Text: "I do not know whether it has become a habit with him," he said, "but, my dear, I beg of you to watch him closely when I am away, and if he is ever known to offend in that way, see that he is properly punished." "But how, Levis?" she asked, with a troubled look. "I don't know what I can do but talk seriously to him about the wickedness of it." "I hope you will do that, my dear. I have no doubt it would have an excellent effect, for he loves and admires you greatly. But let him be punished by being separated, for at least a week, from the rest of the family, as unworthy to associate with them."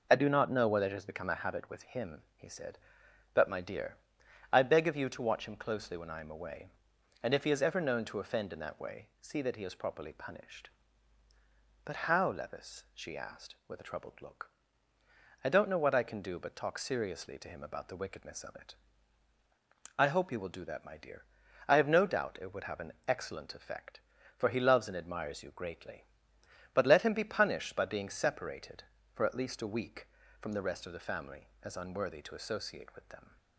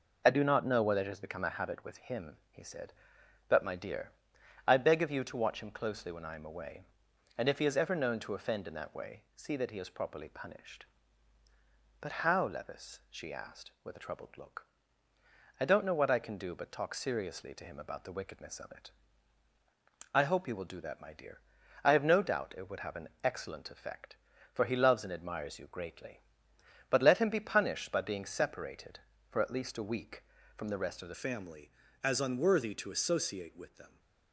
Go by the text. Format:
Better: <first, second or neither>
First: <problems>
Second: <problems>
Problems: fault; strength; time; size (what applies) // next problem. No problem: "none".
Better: first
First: pauses between "an" and "excellent"; slight; at 22.9 s; 0.16 s long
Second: pauses between "an" and "excellent"; slight; at 23.0 s; 0.16 s long // changes voice at "family"; from 31.1 s on; 2.8 s long